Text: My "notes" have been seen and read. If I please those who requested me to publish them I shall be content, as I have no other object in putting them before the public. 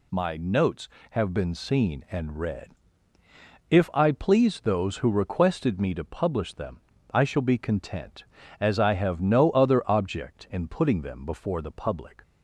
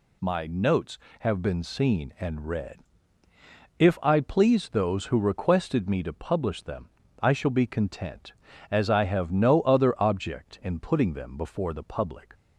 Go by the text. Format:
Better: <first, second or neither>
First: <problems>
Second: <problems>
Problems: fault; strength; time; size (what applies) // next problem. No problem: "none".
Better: neither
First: pauses between "them" and "I"; slight; at 6.7 s; 0.34 s long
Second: pauses between "them" and "I"; slight; at 6.8 s; 0.34 s long